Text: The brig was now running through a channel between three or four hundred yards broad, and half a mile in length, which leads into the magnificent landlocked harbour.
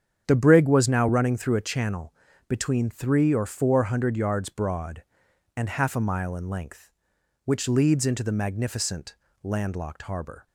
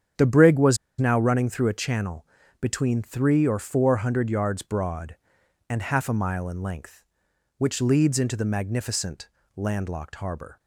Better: first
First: starts louder than the rest; strong; until 1.2 s; 8 dB // pauses between "channel" and "between"; slight; at 2.1 s; 0.34 s long // pauses between "magnificent" and "landlocked"; slight; at 9.1 s; 0.26 s long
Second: starts louder than the rest; strong; until 1.4 s; 8 dB // pauses between "was" and "now"; slight; at 0.7 s; 0.23 s long // pauses between "channel" and "between"; slight; at 2.2 s; 0.34 s long // pauses between "magnificent" and "landlocked"; slight; at 9.2 s; 0.26 s long

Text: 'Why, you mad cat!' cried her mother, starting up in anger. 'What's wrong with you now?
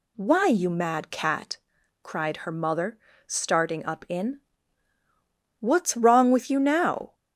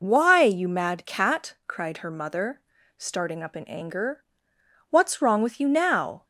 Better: second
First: skips "anger"; at 4.9 s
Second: none

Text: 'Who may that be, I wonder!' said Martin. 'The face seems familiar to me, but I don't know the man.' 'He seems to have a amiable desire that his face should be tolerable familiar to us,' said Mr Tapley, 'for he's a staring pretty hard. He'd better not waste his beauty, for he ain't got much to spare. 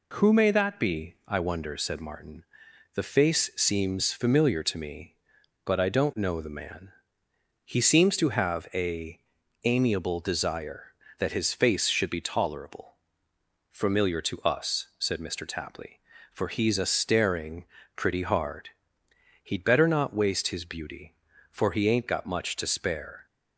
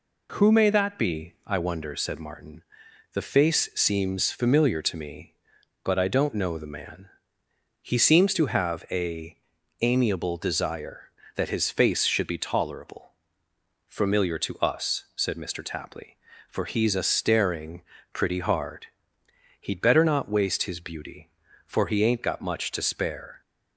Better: neither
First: pauses between "a" and "amiable"; at 9.1 s; 0.44 s long // pauses between "tolerable" and "familiar"; noticeable; at 12.9 s; 0.78 s long // pauses between "staring" and "pretty"; slight; at 17.6 s; 0.32 s long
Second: pauses between "a" and "amiable"; at 9.3 s; 0.44 s long // pauses between "tolerable" and "familiar"; noticeable; at 13.1 s; 0.78 s long // pauses between "staring" and "pretty"; slight; at 17.8 s; 0.32 s long

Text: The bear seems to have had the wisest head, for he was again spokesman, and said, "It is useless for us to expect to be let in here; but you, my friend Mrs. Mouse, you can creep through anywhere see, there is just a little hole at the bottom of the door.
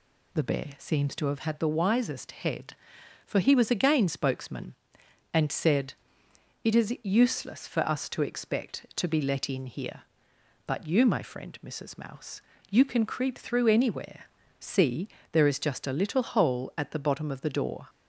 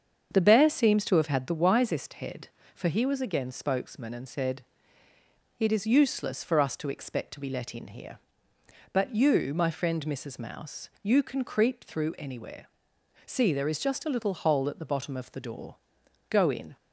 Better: first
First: pauses between "anywhere" and "see"; slight; at 14.2 s; 0.36 s long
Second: starts louder than the rest; strong; until 1.3 s; 7 dB // pauses between "anywhere" and "see"; noticeable; at 12.6 s; 0.58 s long // goes on to say "Go in"; slight; from 16.2 s on; 0.48 s long

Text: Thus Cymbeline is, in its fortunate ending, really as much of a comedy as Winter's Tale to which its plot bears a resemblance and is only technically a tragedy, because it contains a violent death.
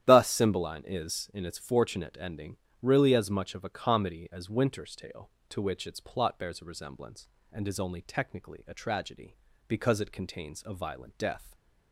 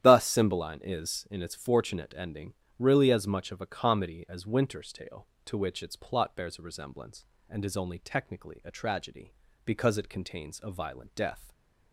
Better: neither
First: starts louder than the rest; strong; until 1.0 s; 11 dB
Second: starts louder than the rest; strong; until 1.0 s; 11 dB

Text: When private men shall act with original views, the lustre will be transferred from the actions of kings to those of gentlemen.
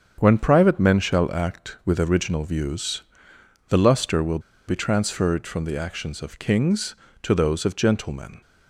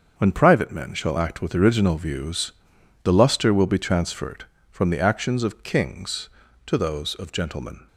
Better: second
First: starts louder than the rest; strong; until 1.2 s; 7.5 dB // pauses between "will" and "be"; slight; at 4.3 s; 0.28 s long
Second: starts louder than the rest; until 1.1 s; 6.5 dB

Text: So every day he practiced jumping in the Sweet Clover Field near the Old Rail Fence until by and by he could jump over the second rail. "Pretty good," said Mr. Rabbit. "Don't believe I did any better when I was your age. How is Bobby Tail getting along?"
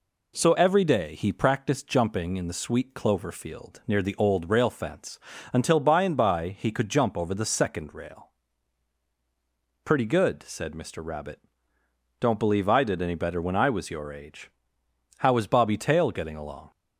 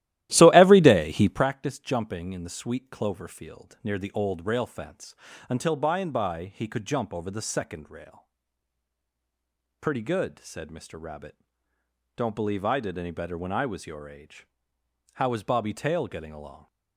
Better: first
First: pauses between "Fence" and "until"; slight; at 5.2 s; 0.32 s long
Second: starts louder than the rest; strong; until 1.5 s; 14.5 dB // pauses between "Fence" and "until"; slight; at 5.1 s; 0.32 s long

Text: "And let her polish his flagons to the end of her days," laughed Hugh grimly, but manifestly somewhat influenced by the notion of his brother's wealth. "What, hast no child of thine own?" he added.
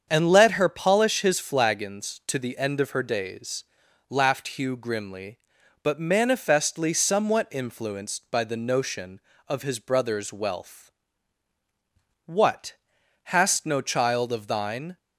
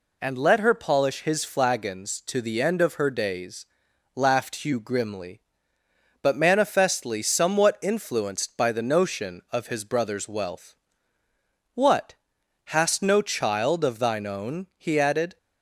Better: second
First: starts louder than the rest; strong; until 1.0 s; 7.5 dB // stops before "own he added"; at 14.9 s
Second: none

